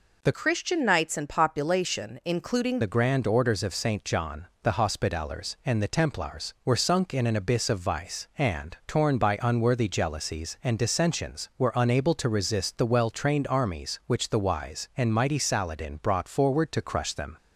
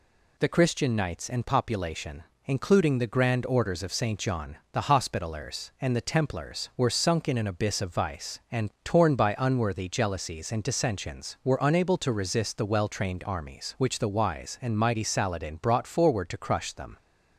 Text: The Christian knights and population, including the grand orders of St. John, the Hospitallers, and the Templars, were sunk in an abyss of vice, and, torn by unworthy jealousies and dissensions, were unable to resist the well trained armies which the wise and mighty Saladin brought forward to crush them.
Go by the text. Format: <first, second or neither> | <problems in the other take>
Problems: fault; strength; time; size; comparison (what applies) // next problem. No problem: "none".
second | changes voice from "Christian" to "including"; from 0.3 to 2.8 s; 2.5 s long